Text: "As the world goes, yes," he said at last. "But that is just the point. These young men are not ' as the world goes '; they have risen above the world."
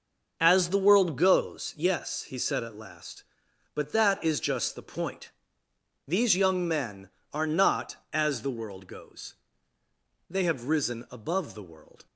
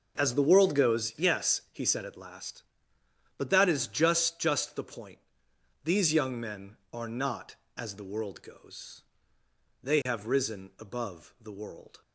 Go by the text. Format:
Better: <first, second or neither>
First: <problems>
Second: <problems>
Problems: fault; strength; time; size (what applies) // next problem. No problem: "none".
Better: first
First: starts louder than the rest; until 1.4 s; 6.5 dB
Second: starts louder than the rest; until 1.2 s; 7 dB // says "just" twice; at 4.3 s